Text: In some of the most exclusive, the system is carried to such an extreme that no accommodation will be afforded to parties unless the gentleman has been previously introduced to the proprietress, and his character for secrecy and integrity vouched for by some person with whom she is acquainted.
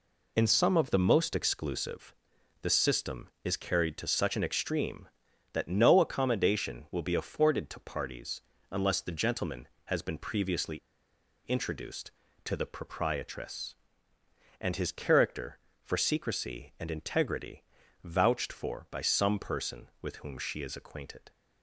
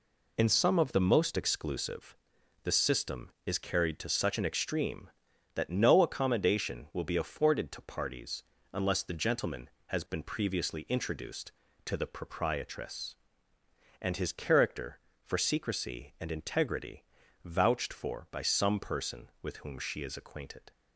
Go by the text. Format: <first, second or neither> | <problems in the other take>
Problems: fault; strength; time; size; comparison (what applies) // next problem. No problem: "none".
second | pauses between "parties" and "unless"; slight; at 8.4 s; 0.32 s long; slight in the second // pauses between "previously" and "introduced"; noticeable; at 10.7 s; 0.66 s long // pauses between "integrity" and "vouched"; at 17.6 s; 0.40 s long; also in the second